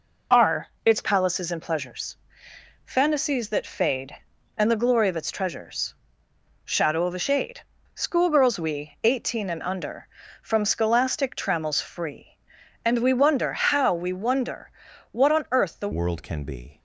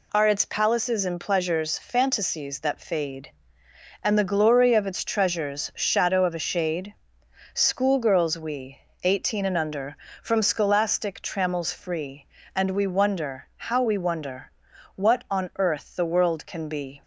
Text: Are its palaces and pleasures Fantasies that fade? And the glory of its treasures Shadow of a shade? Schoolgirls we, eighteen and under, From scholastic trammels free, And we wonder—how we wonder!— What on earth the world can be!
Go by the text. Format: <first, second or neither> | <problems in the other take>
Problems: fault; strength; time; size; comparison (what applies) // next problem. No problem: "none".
second | pauses between "Are" and "its"; slight; at 0.6 s; 0.18 s long // pauses between "pleasures" and "Fantasies"; noticeable; at 2.1 s; 0.70 s long // pauses between "treasures" and "Shadow"; noticeable; at 5.9 s; 0.70 s long // changes voice at "world"; from 15.9 s on; 0.8 s long